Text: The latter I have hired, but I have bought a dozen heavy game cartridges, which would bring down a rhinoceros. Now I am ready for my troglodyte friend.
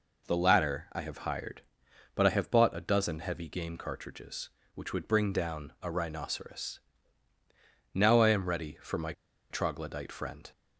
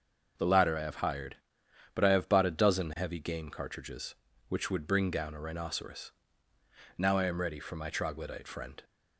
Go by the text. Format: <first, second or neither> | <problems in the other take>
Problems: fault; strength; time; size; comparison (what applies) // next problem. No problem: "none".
second | pauses between "my" and "troglodyte"; at 9.1 s; 0.38 s long